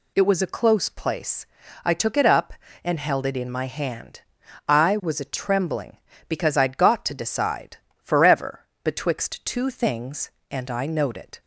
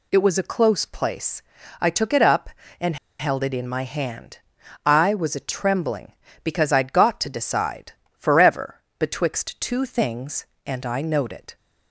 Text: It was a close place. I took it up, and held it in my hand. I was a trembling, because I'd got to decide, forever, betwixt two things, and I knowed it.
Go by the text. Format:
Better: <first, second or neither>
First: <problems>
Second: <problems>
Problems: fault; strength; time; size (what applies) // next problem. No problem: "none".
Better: first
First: none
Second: pauses between "and" and "held"; slight; at 2.9 s; 0.23 s long